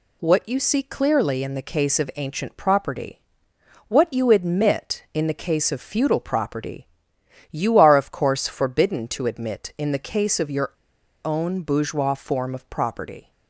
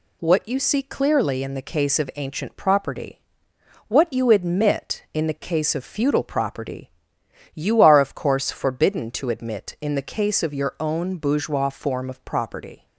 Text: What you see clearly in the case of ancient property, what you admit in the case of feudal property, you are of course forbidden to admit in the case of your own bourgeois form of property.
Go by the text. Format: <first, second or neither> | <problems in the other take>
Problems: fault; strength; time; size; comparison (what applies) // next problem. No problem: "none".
second | pauses between "your" and "own"; noticeable; at 10.7 s; 0.52 s long